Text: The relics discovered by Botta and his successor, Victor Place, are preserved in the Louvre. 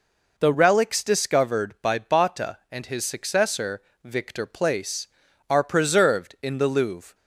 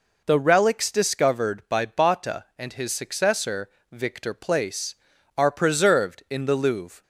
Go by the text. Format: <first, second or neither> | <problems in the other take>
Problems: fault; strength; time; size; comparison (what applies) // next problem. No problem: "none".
neither | none